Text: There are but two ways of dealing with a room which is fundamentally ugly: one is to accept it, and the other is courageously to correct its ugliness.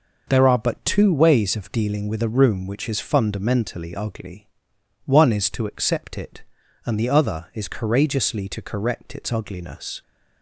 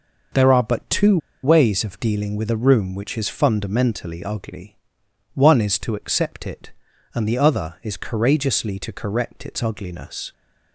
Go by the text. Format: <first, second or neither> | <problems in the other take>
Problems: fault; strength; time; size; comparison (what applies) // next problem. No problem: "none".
first | pauses between "two" and "ways"; slight; at 1.1 s; 0.26 s long